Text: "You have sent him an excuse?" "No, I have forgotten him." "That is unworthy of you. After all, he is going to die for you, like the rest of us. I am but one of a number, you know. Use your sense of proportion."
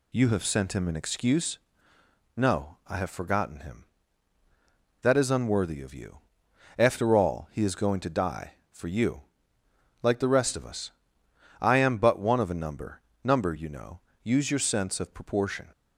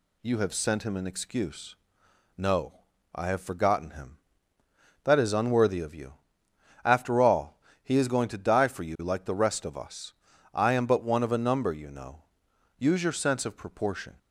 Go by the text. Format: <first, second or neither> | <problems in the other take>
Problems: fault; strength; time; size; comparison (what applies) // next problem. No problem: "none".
second | says "number" twice; at 13.2 s